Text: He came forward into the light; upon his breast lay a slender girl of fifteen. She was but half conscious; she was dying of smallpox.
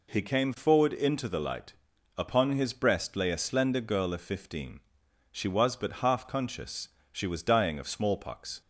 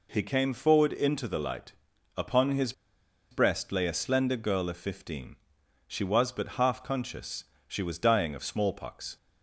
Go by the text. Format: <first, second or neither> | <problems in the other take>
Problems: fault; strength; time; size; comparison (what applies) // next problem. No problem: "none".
first | pauses between "his" and "breast"; noticeable; at 2.7 s; 0.58 s long